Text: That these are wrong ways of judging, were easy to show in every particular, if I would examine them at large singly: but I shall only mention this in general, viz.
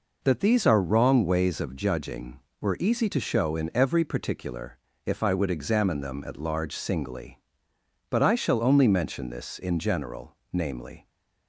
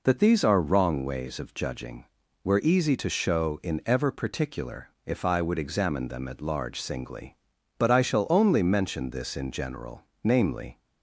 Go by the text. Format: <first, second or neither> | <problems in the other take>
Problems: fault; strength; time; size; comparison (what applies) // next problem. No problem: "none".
first | says "ever" for "every"; at 3.8 s